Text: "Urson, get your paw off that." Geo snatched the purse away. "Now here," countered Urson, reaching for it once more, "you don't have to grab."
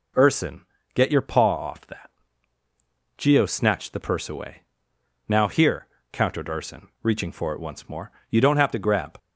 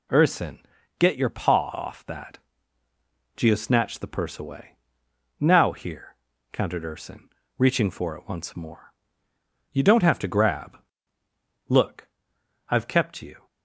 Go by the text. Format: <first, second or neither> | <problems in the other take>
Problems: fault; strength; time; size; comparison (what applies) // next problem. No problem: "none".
first | goes on to say "Look I've kept you"; strong; from 11.7 s on; 1.7 s long